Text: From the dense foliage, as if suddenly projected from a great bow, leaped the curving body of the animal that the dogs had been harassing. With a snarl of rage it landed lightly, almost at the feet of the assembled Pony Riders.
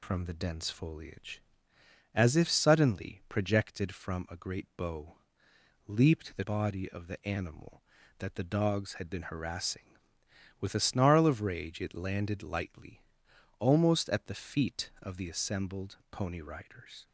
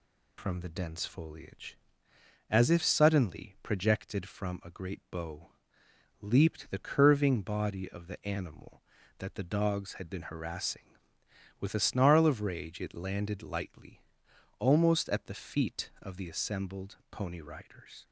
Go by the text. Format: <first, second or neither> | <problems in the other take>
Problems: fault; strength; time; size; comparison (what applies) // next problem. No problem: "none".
second | skips "curving"; at 6.4 s